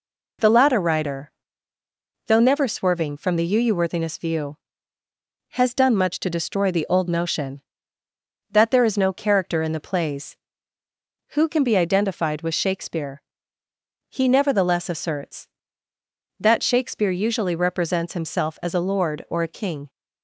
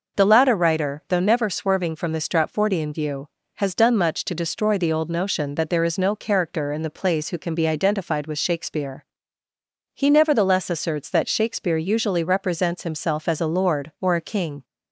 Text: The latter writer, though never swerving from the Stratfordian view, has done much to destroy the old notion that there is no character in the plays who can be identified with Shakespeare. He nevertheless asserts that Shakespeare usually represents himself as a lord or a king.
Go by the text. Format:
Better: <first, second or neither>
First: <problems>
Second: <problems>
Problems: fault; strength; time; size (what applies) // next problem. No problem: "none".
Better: second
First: says "Uuworthiness" for "Stratfordian"; at 3.5 s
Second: none